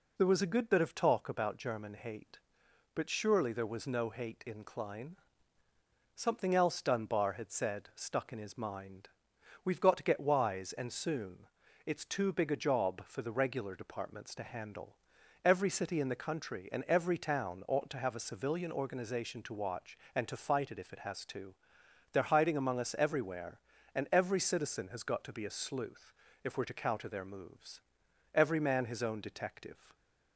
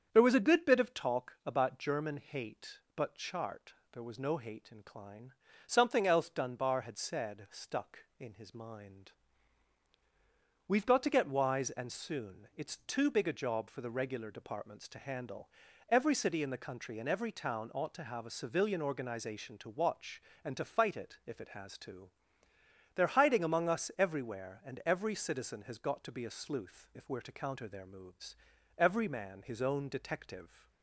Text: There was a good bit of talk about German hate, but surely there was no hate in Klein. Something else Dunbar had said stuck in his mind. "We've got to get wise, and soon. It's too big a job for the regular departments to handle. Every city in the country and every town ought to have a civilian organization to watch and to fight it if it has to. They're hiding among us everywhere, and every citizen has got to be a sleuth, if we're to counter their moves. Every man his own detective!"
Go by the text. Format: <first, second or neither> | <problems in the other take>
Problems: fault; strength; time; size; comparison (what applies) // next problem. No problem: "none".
first | starts louder than the rest; strong; until 1.1 s; 7.5 dB // says "chart" for "surely"; at 3.1 s